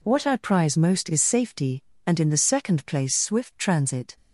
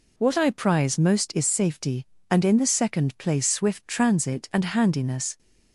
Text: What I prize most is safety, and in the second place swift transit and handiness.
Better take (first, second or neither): second